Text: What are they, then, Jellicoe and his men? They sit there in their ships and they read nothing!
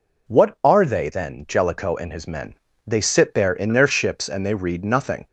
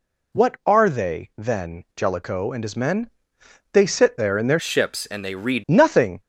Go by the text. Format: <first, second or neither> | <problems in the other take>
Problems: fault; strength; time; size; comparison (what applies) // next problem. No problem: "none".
first | changes voice from "ships" to "read"; from 4.5 to 5.6 s; 1.1 s long